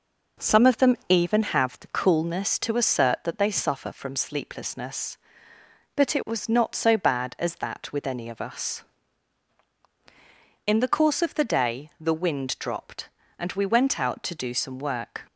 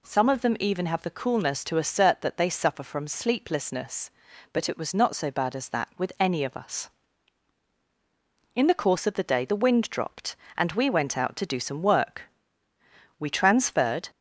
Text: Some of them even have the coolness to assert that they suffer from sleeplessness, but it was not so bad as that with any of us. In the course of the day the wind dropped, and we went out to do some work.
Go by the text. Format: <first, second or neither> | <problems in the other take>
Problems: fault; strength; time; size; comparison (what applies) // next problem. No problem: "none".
first | goes on to say "We transferred"; noticeable; from 13.1 s on; 0.90 s long